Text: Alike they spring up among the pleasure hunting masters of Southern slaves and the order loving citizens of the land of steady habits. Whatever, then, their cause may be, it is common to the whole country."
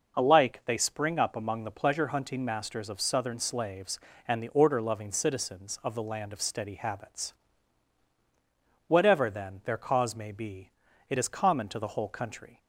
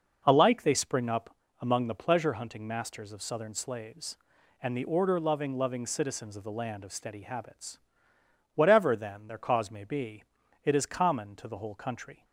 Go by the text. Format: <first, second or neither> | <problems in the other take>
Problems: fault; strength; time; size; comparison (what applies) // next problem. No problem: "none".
first | pauses between "up" and "among"; slight; at 1.3 s; 0.24 s long // says "loving" twice; at 5.5 s